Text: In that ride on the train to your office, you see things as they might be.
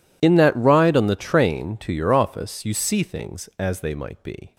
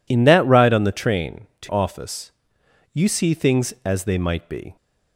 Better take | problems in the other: first | skips "your"; at 1.7 s

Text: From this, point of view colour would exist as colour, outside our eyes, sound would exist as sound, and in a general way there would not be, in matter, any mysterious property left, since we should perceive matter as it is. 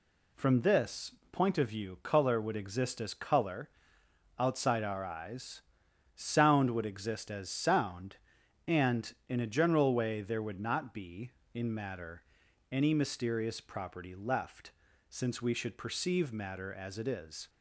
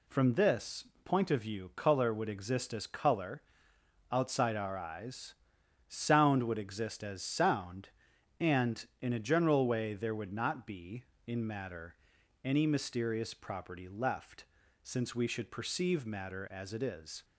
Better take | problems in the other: neither | none

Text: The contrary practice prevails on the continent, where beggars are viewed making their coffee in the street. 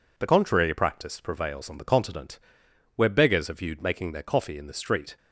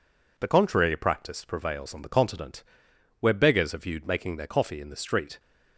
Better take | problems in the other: neither | none

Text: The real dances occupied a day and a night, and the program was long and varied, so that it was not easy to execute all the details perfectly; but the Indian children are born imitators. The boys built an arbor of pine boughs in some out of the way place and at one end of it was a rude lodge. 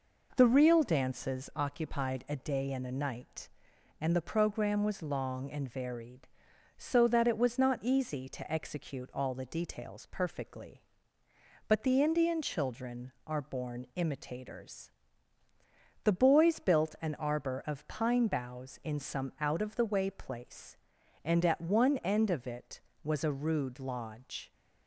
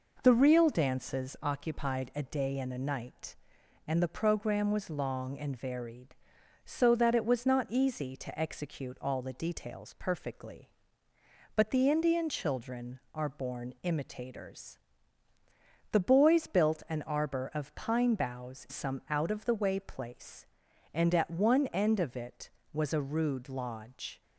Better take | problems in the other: first | skips "in"; at 18.6 s

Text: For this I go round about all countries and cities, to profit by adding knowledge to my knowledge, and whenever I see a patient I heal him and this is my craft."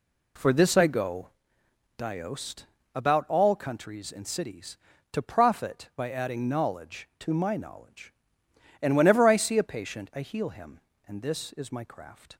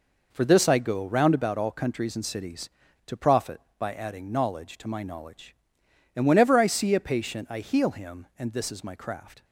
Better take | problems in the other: second | says "diost" for "round"; at 1.9 s

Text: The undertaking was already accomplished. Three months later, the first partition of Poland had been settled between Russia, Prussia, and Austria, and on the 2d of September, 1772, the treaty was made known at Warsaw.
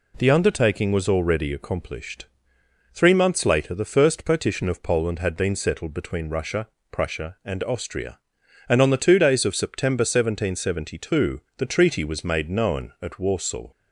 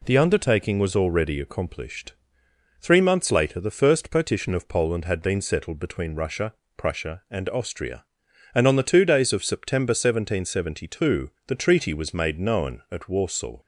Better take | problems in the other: neither | none

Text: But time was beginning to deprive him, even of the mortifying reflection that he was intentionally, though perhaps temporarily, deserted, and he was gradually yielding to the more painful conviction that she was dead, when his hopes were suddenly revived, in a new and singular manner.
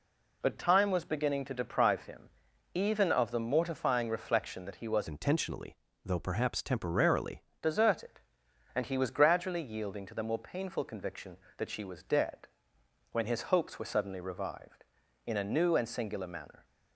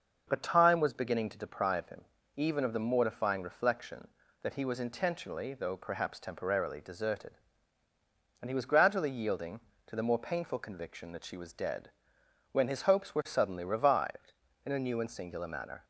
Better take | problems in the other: second | changes voice from "intentionally" to "temporarily"; from 5.0 to 7.4 s; 2.4 s long

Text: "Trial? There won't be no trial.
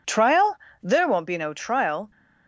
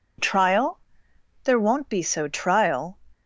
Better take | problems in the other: first | says "so" for "no"; at 2.0 s

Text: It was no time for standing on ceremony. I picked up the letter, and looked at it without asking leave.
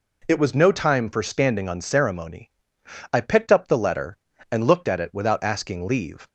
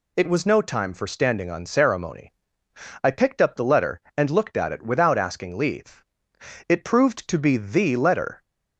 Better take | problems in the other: first | goes on to say "It proved to be the letter"; strong; from 6.6 s on; 1.7 s long

